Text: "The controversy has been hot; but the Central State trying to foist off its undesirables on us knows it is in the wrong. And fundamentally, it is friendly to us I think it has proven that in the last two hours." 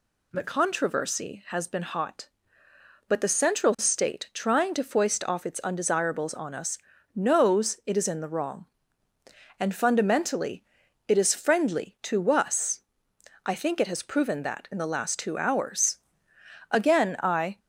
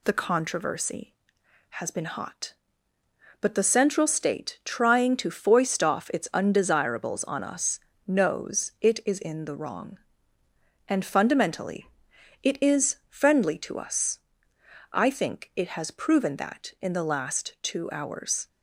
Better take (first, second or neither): second